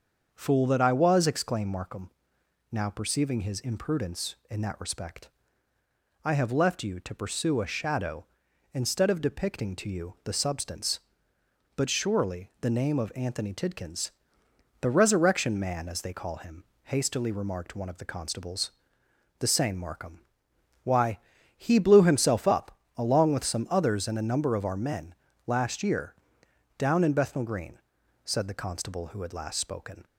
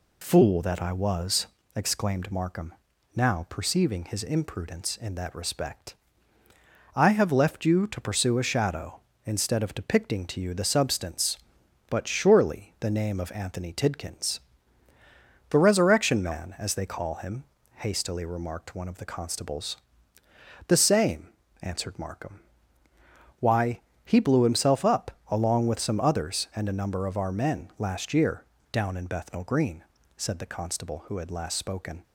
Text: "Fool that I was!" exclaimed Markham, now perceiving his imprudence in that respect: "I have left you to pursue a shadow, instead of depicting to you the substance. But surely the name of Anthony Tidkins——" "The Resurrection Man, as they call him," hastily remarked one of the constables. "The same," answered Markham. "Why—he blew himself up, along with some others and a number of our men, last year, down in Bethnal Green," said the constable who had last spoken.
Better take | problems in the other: second | starts louder than the rest; until 1.3 s; 6.5 dB // skips "answered"; at 19.7 s

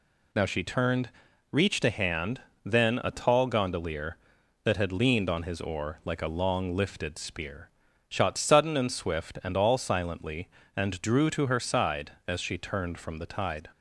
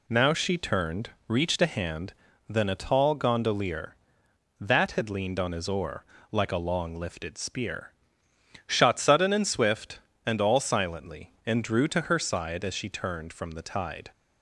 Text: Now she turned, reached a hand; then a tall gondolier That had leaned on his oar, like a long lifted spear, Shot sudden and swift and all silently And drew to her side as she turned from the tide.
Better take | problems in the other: neither | none

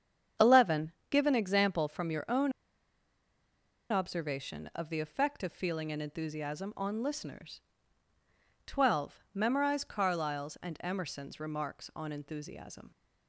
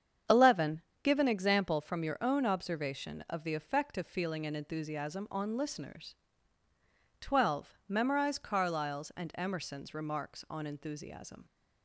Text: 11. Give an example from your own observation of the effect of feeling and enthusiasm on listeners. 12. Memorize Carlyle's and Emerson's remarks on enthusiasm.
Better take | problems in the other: second | starts louder than the rest; strong; until 1.6 s; 8 dB; strong in the second // pauses between "own" and "observation"; strong; at 2.5 s; 1.3 s long

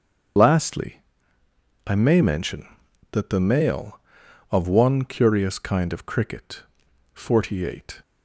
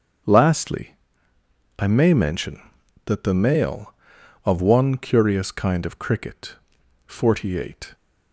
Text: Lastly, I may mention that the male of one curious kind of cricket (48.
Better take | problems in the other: second | loses the start of "Lastly"; at 0.3 s; 45 ms // starts louder than the rest; until 2.2 s; 7 dB; also in the second

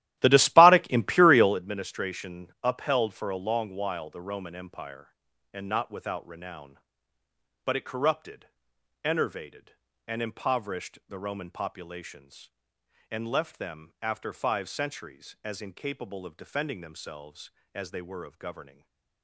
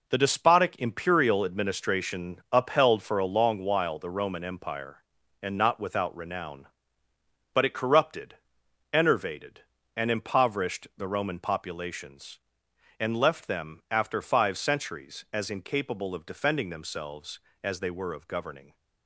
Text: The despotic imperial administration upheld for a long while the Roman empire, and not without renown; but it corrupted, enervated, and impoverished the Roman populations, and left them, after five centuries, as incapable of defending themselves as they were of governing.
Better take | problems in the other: second | starts louder than the rest; strong; until 1.6 s; 14 dB // stays silent after the last word; slight; from 18.7 s on; 0.5 s long

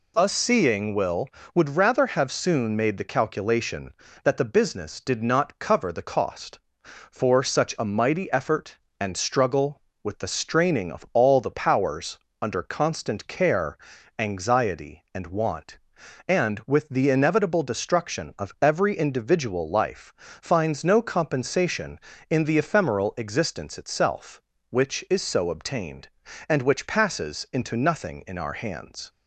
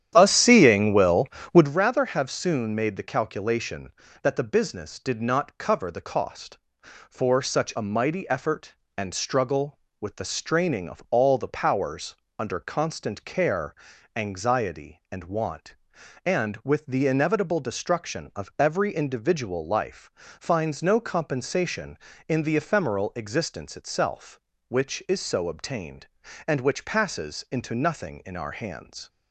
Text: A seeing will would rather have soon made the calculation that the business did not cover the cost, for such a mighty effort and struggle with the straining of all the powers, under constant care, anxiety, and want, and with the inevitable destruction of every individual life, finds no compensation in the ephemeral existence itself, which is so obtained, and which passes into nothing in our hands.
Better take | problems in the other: first | starts louder than the rest; strong; until 1.7 s; 10 dB

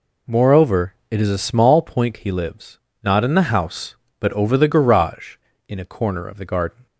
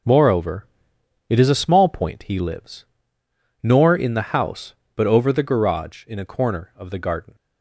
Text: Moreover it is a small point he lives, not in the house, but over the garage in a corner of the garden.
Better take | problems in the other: first | pauses between "Moreover" and "it"; noticeable; at 0.6 s; 0.62 s long // says "nor" for "not"; at 3.6 s

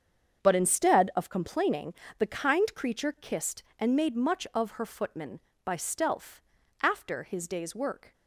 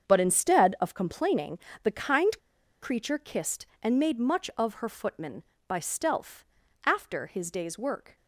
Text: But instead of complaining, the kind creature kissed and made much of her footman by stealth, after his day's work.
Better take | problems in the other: first | starts louder than the rest; strong; until 1.1 s; 7 dB; strong in the first // pauses between "kind" and "creature"; at 2.3 s; 0.42 s long

